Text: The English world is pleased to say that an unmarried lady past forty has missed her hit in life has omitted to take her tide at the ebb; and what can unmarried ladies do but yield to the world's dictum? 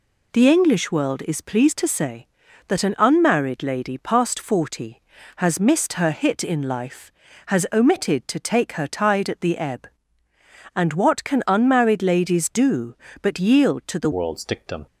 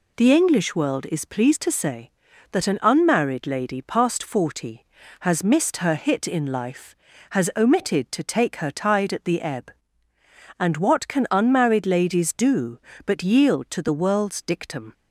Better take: second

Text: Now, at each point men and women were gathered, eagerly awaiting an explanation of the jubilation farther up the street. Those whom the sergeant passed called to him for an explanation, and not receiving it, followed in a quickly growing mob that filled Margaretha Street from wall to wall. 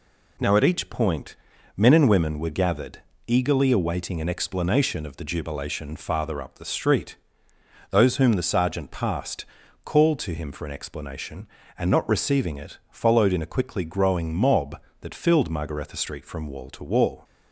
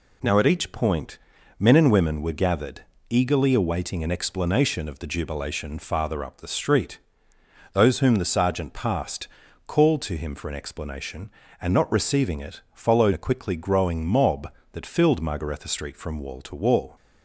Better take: first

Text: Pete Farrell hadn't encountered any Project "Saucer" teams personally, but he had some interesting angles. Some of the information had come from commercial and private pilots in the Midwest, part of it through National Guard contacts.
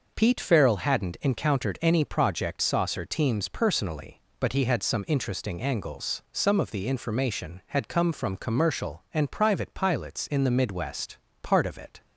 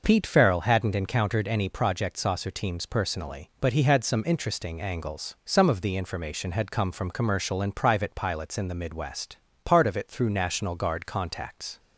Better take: second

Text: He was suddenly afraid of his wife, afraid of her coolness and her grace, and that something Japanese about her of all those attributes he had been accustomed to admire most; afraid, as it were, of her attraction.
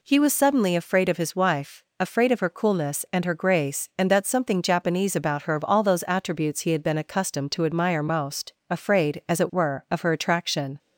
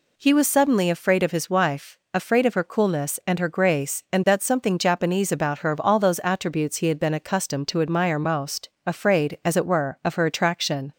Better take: neither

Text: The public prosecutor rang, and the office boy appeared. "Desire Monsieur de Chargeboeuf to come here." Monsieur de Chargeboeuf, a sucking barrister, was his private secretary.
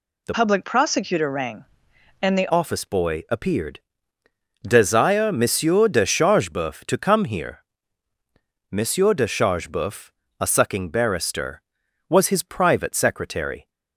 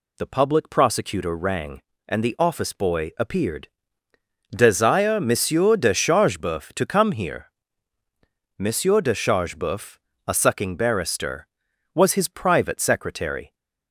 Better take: second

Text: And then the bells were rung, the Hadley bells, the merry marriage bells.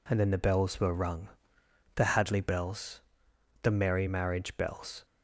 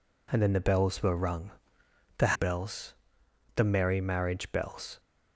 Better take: first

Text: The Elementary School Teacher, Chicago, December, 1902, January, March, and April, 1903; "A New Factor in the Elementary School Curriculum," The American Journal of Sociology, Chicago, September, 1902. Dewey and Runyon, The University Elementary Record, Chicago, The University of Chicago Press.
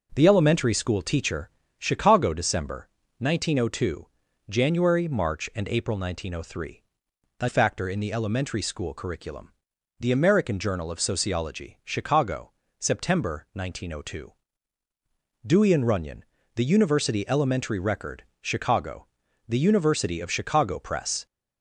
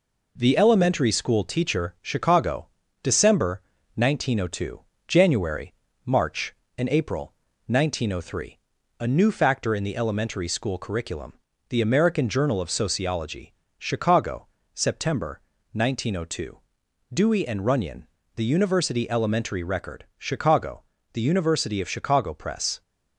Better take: second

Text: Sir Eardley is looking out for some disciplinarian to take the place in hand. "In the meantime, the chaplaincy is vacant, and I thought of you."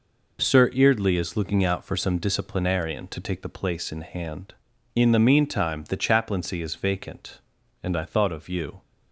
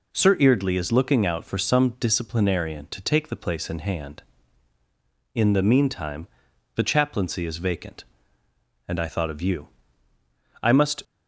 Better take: first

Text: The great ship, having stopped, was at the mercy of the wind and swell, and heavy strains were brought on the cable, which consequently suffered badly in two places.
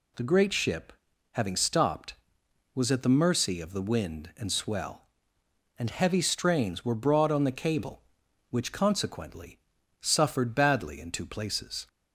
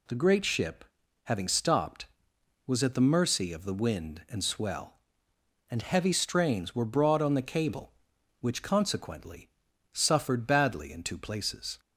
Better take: neither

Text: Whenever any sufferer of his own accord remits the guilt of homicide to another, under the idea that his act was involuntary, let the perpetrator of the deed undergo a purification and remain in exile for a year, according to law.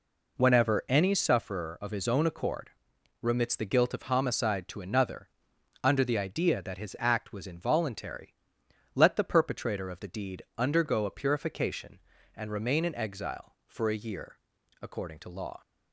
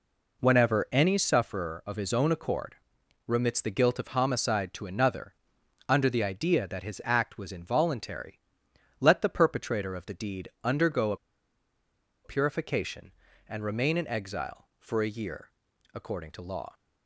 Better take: first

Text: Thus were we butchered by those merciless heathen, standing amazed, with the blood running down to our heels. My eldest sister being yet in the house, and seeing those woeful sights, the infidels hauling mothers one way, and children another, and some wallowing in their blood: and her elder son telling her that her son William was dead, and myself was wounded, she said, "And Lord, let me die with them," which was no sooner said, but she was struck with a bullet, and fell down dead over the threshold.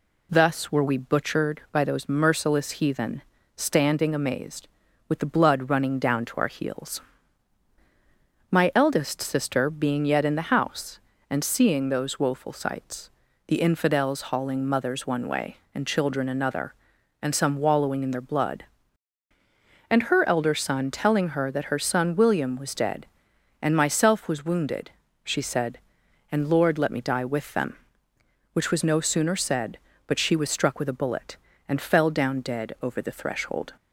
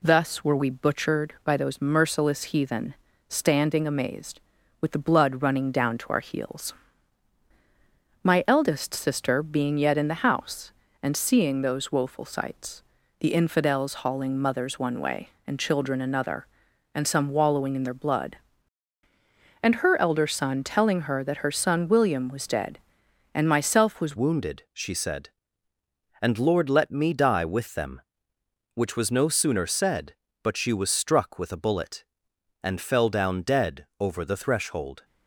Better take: first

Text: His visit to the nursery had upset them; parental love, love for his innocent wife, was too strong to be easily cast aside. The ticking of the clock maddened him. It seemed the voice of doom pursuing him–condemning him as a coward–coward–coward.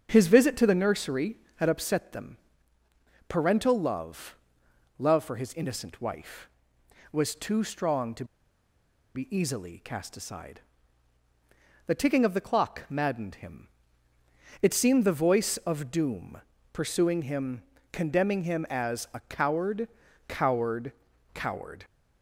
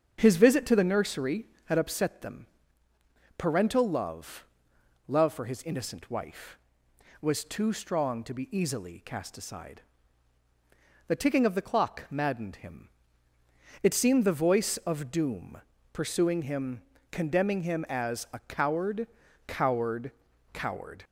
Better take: second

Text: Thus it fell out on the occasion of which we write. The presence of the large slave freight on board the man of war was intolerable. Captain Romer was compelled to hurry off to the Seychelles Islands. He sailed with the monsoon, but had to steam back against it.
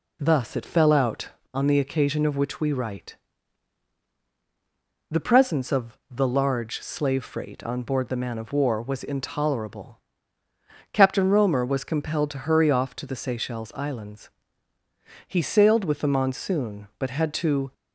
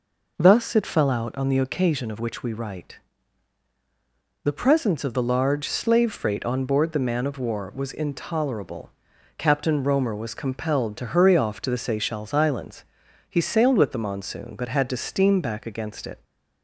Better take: second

